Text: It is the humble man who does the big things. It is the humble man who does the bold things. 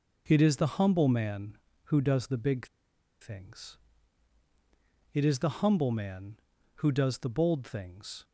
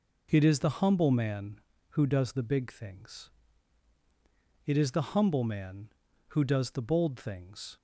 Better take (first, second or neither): second